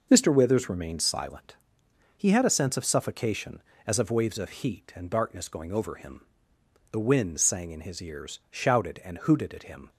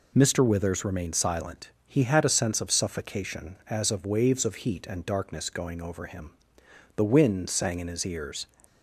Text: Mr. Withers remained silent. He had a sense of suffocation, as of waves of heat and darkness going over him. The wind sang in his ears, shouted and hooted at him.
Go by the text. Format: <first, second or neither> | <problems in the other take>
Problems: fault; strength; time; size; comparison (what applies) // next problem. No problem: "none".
first | stops before "shouted and hooted at him"; at 8.6 s